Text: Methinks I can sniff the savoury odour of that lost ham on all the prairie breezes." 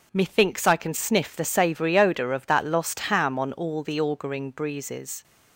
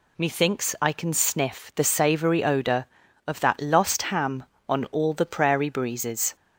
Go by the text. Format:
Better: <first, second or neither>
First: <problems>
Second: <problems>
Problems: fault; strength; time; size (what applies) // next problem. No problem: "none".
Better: second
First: says "auguring" for "prairie"; at 4.0 s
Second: none